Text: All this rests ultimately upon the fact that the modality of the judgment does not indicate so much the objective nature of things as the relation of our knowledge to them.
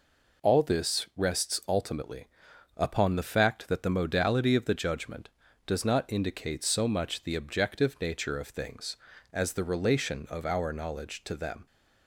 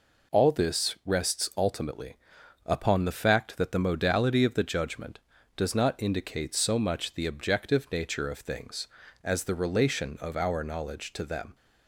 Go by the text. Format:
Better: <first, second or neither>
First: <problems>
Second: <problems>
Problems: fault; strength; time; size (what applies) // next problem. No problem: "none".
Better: neither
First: pauses between "ultimately" and "upon"; noticeable; at 2.2 s; 0.48 s long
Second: pauses between "ultimately" and "upon"; noticeable; at 2.1 s; 0.48 s long